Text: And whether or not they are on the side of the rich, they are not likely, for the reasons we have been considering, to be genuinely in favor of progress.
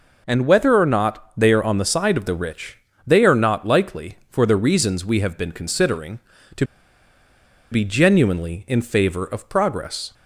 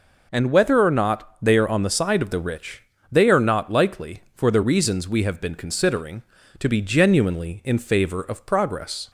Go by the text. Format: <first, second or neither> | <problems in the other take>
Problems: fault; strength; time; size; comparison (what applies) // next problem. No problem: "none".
second | pauses between "to" and "be"; at 6.6 s; 1.0 s long